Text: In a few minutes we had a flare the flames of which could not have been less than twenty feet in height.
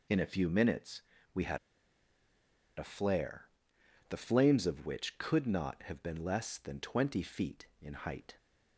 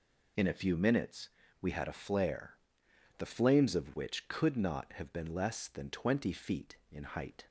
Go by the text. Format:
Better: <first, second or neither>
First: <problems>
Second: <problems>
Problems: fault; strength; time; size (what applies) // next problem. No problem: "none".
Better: second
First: pauses between "minutes" and "we"; slight; at 1.0 s; 0.32 s long // pauses between "had" and "a"; at 1.5 s; 1.2 s long // pauses between "flare" and "the"; noticeable; at 3.4 s; 0.62 s long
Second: pauses between "minutes" and "we"; slight; at 1.2 s; 0.32 s long // pauses between "flare" and "the"; noticeable; at 2.5 s; 0.62 s long